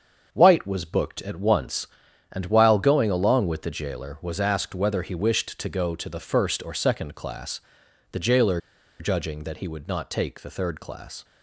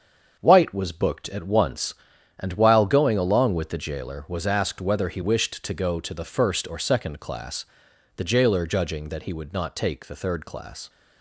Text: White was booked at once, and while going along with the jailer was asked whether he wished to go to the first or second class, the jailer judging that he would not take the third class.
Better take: second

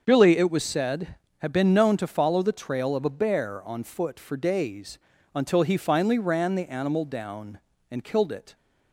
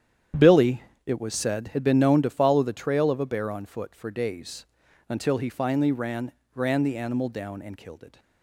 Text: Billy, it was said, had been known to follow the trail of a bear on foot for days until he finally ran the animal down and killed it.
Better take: first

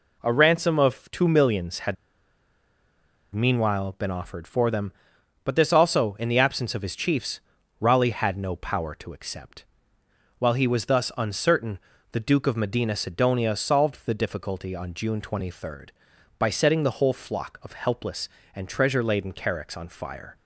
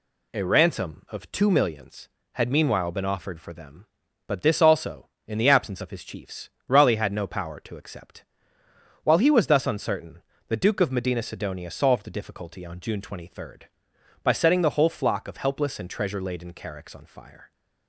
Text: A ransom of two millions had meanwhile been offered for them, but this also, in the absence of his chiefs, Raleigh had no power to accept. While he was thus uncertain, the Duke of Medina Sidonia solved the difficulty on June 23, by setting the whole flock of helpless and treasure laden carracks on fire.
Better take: second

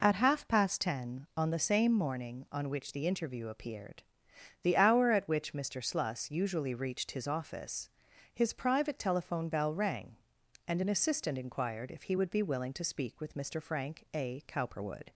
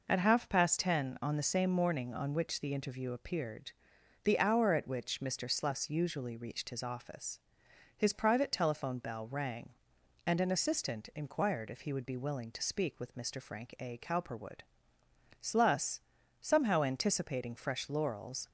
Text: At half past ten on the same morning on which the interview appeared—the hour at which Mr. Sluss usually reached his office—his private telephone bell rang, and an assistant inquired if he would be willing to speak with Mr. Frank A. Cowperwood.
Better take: first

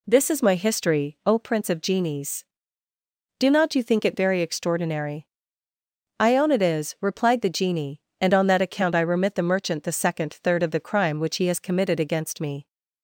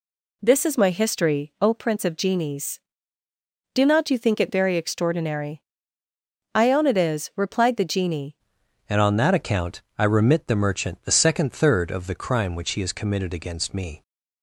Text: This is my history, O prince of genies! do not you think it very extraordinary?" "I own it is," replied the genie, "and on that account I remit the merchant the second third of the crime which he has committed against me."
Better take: first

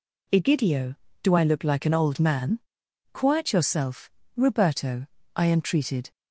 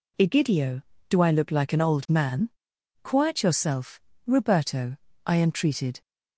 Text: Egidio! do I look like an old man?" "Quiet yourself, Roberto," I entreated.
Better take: neither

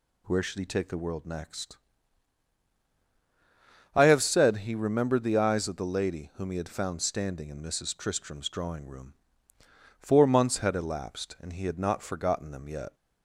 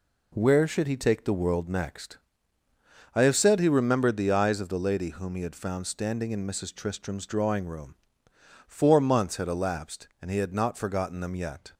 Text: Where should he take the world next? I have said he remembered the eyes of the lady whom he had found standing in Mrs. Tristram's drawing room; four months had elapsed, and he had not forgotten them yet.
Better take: neither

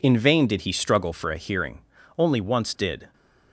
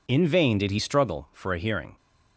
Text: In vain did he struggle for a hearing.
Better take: second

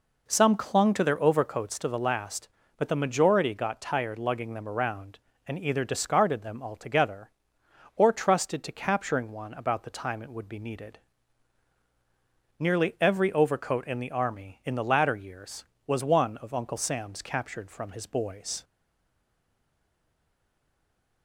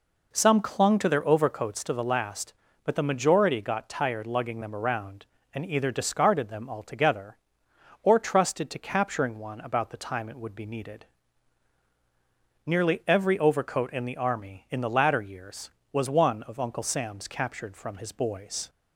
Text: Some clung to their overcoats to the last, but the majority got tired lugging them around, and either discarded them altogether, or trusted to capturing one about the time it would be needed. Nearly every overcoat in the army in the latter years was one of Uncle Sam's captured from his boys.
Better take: second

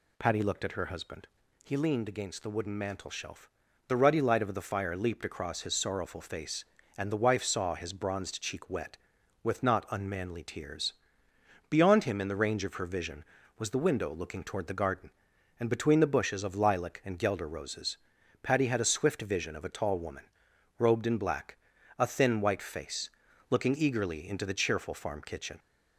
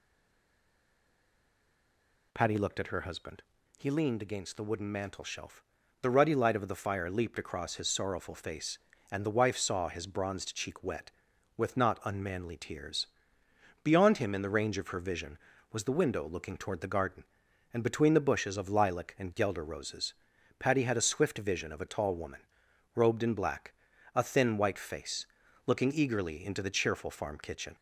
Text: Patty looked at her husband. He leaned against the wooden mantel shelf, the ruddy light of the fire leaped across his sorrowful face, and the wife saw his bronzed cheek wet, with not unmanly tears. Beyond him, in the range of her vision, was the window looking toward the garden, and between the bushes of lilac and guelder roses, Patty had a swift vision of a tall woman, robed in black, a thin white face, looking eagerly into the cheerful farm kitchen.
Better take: first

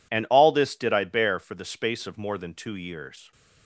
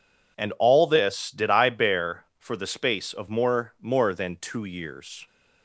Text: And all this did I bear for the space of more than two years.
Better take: first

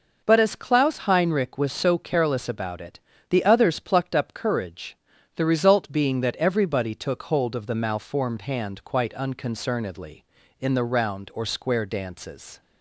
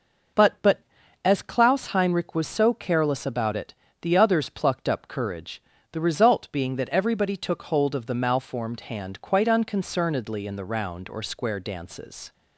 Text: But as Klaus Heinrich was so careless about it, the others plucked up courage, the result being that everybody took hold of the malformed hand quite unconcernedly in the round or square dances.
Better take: first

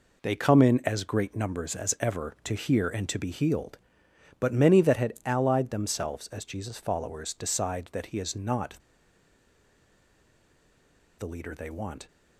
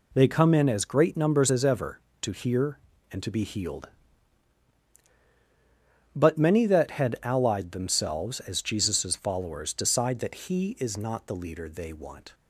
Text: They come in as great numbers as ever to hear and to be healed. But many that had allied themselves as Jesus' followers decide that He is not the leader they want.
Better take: second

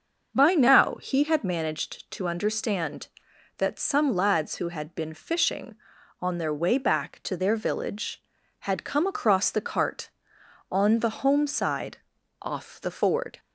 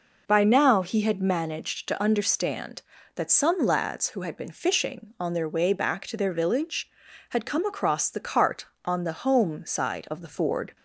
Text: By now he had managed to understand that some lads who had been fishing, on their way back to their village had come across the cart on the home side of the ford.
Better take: second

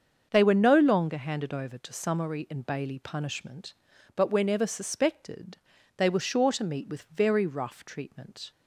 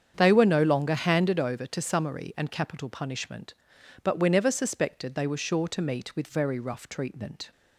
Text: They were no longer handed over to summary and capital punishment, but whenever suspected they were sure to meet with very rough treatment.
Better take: second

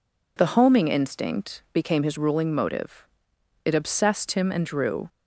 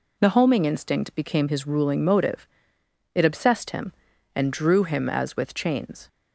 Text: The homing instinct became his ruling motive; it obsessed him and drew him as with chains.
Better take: second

